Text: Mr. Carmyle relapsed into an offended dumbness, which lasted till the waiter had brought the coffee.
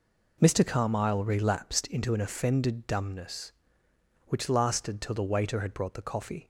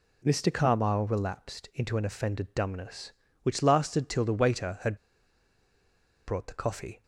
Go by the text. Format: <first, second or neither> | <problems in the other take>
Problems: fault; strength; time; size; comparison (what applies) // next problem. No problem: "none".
first | pauses between "had" and "brought"; strong; at 4.9 s; 1.3 s long